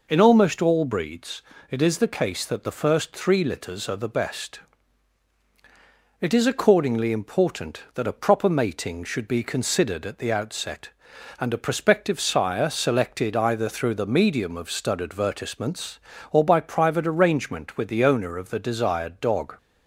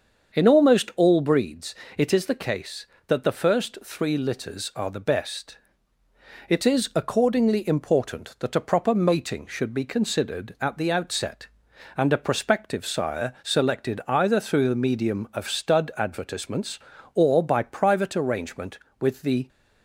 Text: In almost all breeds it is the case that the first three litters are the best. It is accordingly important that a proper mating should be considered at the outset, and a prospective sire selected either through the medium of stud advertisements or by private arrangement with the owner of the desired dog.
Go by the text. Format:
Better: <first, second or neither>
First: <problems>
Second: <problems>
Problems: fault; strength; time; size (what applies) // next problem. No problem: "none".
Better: first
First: pauses between "breeds" and "it"; slight; at 1.4 s; 0.28 s long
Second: starts louder than the rest; until 1.4 s; 7 dB // pauses between "breeds" and "it"; slight; at 1.7 s; 0.22 s long // stops before "owner of the desired dog"; at 19.4 s